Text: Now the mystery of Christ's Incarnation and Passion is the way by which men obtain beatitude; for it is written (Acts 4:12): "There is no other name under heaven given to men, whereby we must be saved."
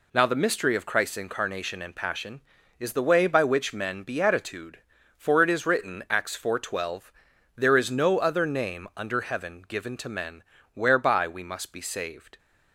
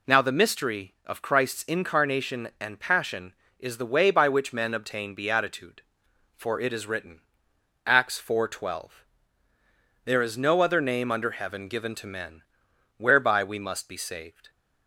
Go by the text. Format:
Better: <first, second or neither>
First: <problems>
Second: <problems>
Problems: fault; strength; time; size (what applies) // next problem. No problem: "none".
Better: second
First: skips "obtain"; at 4.0 s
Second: none